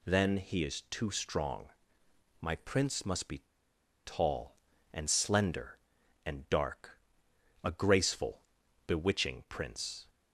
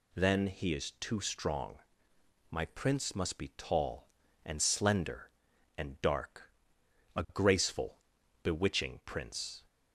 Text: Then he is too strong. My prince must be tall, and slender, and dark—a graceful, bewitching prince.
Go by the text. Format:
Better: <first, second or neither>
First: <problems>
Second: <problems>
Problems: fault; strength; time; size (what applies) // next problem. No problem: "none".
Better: second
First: pauses between "be" and "tall"; noticeable; at 3.4 s; 0.61 s long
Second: none